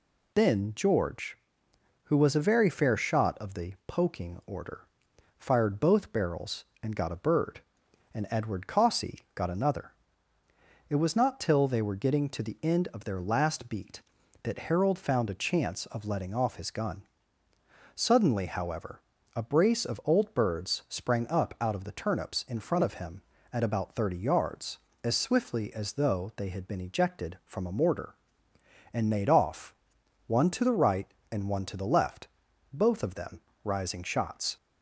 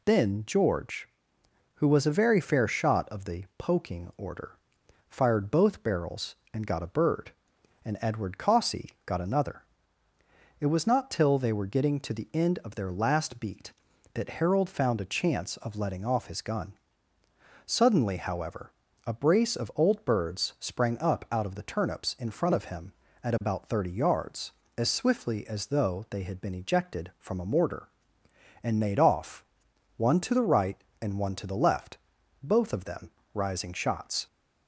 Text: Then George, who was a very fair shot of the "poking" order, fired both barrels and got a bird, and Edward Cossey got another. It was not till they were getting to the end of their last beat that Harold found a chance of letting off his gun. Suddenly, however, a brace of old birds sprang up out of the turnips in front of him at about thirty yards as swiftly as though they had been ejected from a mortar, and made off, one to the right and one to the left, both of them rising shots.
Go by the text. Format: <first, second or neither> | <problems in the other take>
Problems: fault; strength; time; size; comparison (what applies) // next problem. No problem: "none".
neither | pauses between "them" and "rising"; slight; the same in both